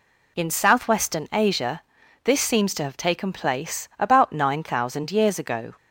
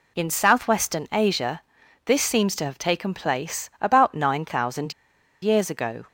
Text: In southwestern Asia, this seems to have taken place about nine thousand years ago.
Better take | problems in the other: first | pauses between "thousand" and "years"; noticeable; at 4.9 s; 0.50 s long

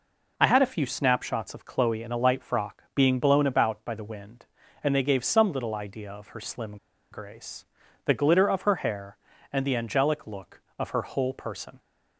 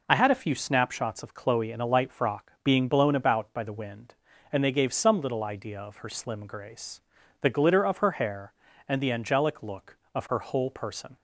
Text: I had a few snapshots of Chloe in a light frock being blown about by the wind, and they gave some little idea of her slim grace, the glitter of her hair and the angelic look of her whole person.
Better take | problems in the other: second | pauses between "slim" and "grace"; slight; at 6.7 s; 0.36 s long

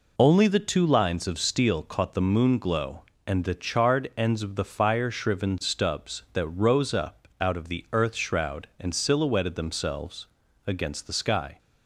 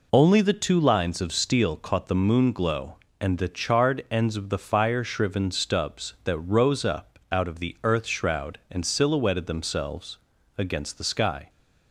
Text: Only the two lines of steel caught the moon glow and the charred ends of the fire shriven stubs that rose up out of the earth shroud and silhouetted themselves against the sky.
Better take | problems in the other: neither | pauses between "themselves" and "against"; the same in both

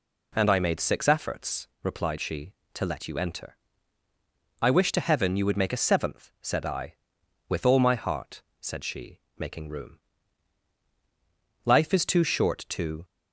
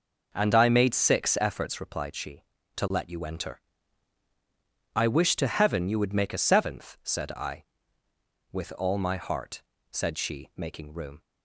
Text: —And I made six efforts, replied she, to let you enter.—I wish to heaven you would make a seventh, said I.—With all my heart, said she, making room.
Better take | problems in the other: second | goes on to say "Life is too short to"; from 11.6 s on; 1.4 s long

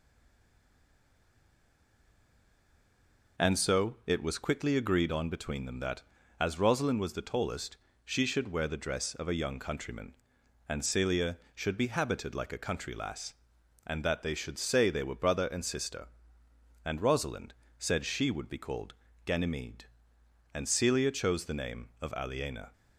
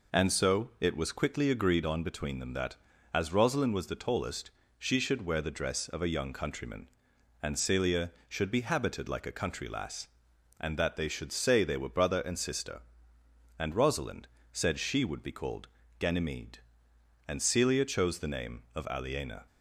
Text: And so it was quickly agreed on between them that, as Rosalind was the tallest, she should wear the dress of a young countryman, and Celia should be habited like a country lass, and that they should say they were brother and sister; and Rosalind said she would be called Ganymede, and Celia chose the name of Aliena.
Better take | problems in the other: second | stays silent before the first word; strong; until 3.3 s; 3.3 s long // pauses between "Rosalind" and "said"; slight; at 17.5 s; 0.24 s long; slight in the second // pauses between "called" and "Ganymede"; slight; at 18.9 s; 0.32 s long; slight in the second

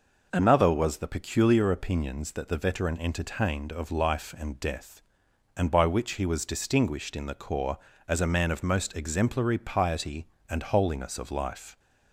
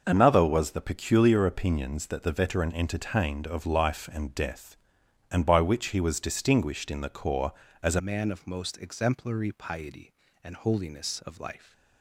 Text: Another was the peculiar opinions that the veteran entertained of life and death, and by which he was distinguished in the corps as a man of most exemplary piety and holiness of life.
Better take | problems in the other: first | changes voice at "man"; from 7.9 s on; 3.8 s long

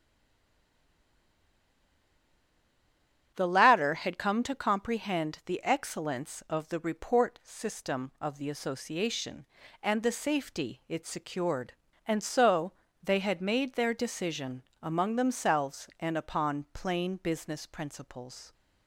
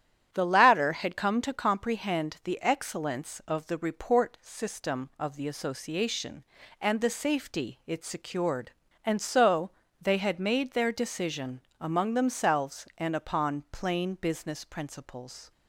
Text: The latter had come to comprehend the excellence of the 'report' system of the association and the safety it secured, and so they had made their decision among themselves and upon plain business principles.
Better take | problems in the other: second | stays silent before the first word; strong; until 3.3 s; 3.3 s long // starts louder than the rest; strong; until 4.3 s; 10 dB; strong in the second // pauses between "so" and "they"; slight; at 12.7 s; 0.30 s long; slight in the second // pauses between "decision" and "among"; slight; at 14.6 s; 0.22 s long; slight in the second

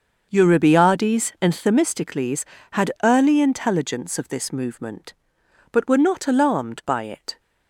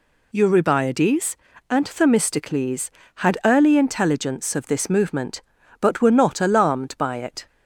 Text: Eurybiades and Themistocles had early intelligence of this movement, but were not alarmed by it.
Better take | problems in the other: second | starts louder than the rest; until 1.6 s; 6.5 dB

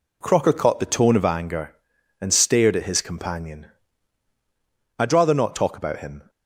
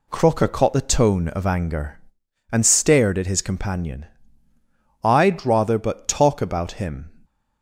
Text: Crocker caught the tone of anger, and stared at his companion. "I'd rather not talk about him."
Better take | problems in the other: first | says "but" for "not"; at 5.7 s

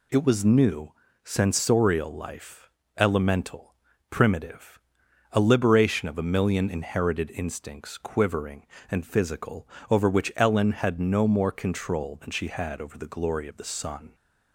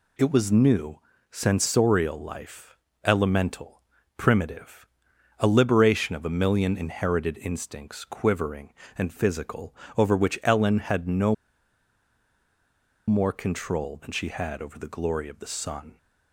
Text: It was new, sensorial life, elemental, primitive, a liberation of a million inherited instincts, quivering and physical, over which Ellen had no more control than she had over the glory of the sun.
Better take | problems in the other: first | pauses between "no" and "more"; strong; at 11.3 s; 1.7 s long

